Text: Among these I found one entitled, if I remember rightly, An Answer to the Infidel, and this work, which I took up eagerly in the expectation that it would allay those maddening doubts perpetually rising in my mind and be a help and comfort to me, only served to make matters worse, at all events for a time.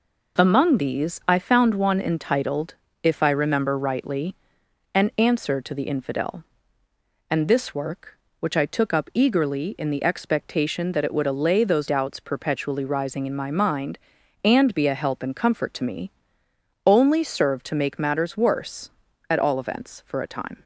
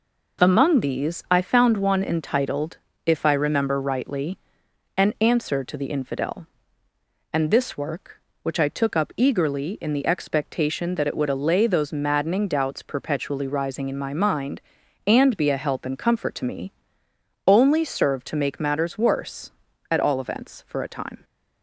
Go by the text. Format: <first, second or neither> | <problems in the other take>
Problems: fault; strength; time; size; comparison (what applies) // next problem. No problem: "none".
second | skips "maddening"; at 11.8 s